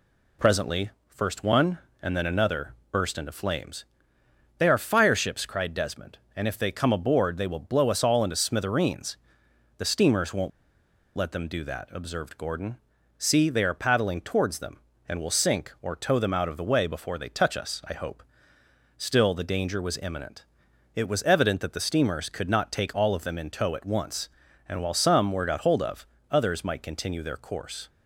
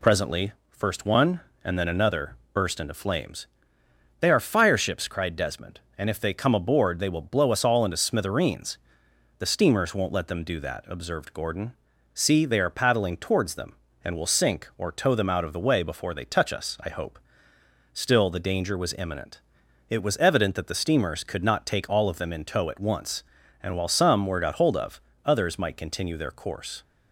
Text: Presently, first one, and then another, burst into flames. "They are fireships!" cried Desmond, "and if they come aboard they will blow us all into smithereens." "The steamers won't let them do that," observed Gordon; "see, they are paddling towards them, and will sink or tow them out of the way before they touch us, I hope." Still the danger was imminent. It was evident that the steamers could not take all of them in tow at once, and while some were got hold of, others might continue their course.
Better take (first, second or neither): second